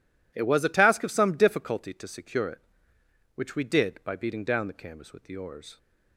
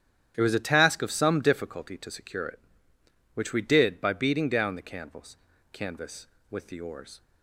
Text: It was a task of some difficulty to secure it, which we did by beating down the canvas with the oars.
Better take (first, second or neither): first